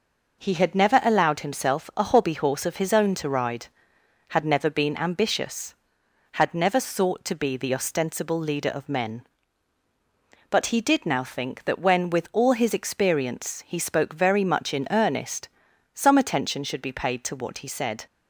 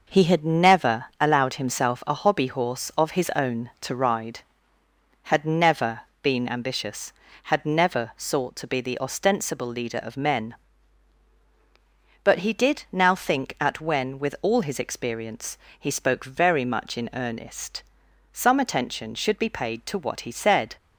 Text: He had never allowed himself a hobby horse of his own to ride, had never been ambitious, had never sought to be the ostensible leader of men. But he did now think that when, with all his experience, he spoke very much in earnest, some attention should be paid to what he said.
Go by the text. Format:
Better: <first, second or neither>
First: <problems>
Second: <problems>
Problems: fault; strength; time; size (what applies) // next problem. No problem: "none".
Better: first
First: none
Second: pauses between "never" and "been"; slight; at 6.0 s; 0.20 s long // says "at" for "that"; at 13.5 s